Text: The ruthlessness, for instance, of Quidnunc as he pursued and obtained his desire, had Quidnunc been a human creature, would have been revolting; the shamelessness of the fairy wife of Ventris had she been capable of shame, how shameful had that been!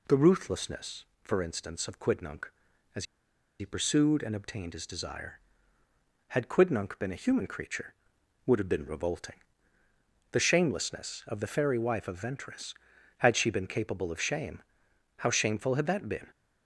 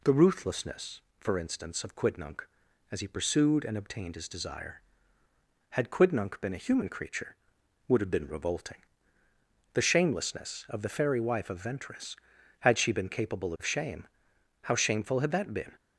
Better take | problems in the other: second | pauses between "as" and "he"; noticeable; at 3.0 s; 0.54 s long

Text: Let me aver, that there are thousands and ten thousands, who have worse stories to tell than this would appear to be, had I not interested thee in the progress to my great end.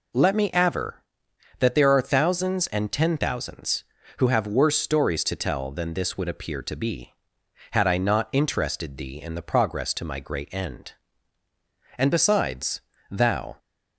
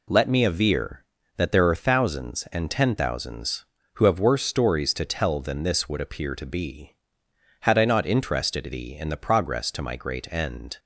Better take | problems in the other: second | goes on to say "And besides thou"; from 11.9 s on; 1.6 s long

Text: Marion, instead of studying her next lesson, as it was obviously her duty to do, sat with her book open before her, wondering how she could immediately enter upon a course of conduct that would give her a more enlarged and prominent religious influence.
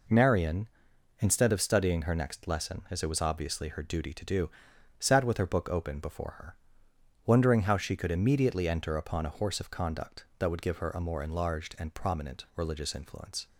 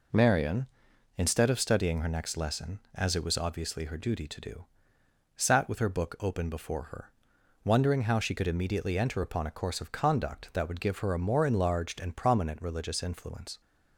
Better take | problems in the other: second | says "horse" for "course"; at 9.3 s

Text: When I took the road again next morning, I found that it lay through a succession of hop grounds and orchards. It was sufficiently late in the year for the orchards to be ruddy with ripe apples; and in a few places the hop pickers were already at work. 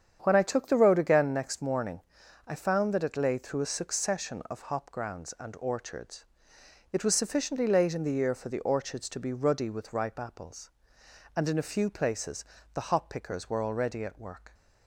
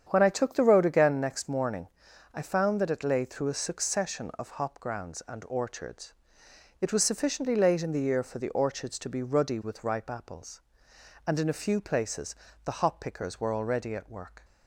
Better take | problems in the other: neither | starts louder than the rest; strong; the same in both // pauses between "places" and "the"; slight; the same in both

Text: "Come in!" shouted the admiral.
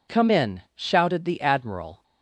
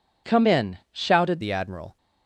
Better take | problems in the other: first | changes voice at "the"; from 1.4 s on; 0.5 s long

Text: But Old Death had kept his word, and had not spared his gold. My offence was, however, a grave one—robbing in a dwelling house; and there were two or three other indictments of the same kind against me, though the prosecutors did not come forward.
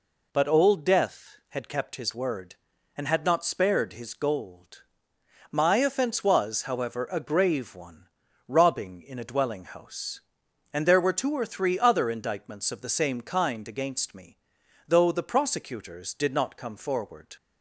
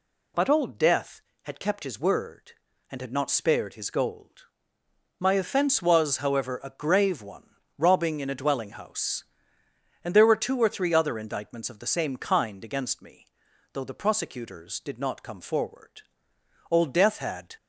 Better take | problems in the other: first | goes on to say "Old Death had"; noticeable; from 16.6 s on; 0.86 s long

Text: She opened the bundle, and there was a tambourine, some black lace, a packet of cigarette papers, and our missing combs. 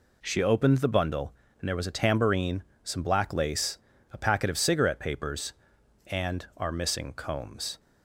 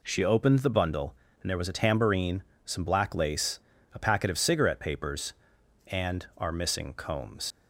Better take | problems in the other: first | leaves "combs" unfinished; at 7.5 s; 95 ms

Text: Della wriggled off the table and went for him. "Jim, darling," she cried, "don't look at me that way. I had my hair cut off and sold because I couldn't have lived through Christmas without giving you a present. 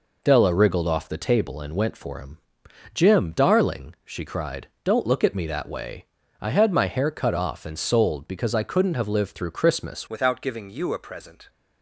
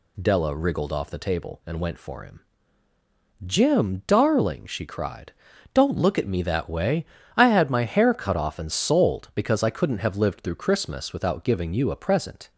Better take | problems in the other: second | changes voice at "without"; from 10.0 s on; 1.4 s long

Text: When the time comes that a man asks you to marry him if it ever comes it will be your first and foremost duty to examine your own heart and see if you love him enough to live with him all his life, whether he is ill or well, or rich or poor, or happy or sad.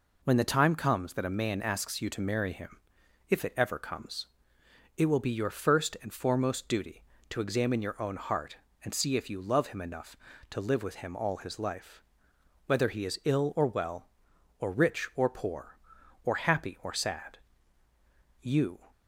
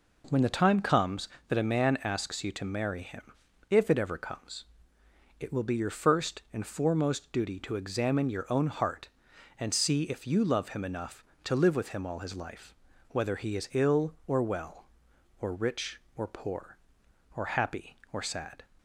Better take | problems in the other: second | pauses between "him" and "if"; noticeable; at 2.7 s; 0.52 s long; also in the second // pauses between "comes" and "it"; noticeable; at 4.2 s; 0.72 s long; noticeable in the second // goes on to say "You"; slight; from 18.4 s on; 0.38 s long

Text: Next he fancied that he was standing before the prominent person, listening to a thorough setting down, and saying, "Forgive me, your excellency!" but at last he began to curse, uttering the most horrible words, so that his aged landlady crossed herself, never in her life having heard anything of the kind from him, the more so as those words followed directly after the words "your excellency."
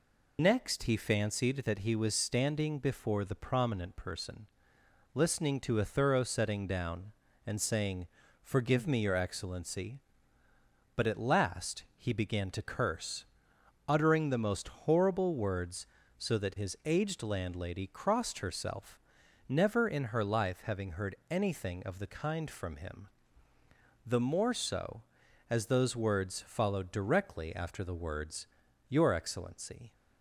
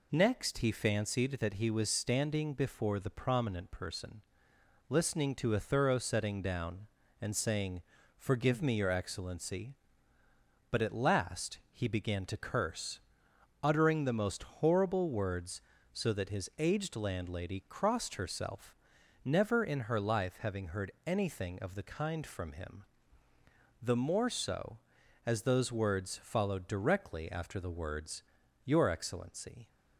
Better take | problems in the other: second | loses the start of "Next"; at 0.3 s; 25 ms // pauses between "heard" and "anything"; slight; at 21.1 s; 0.16 s long; slight in the second // pauses between "words" and "your"; at 28.4 s; 0.42 s long; also in the second

